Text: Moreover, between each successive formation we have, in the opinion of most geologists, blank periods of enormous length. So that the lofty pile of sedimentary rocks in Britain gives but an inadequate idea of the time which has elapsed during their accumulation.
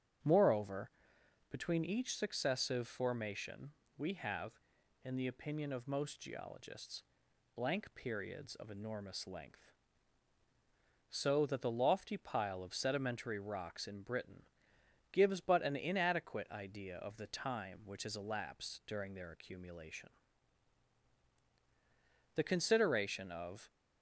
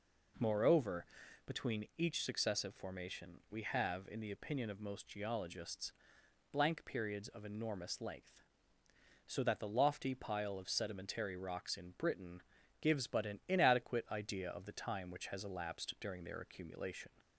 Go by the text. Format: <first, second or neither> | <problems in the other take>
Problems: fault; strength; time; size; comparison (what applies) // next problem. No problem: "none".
second | starts louder than the rest; strong; until 1.8 s; 8 dB // pauses between "formation" and "we"; slight; at 3.7 s; 0.26 s long // pauses between "Britain" and "gives"; noticeable; at 14.4 s; 0.68 s long; also in the second // goes on to say "The consideration of"; from 22.3 s on; 1.3 s long